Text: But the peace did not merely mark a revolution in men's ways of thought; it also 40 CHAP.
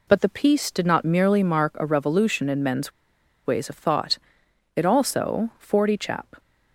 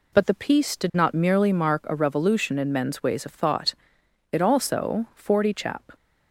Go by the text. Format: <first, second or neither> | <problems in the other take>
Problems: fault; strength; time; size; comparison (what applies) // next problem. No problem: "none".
second | pauses between "men's" and "ways"; noticeable; at 2.9 s; 0.53 s long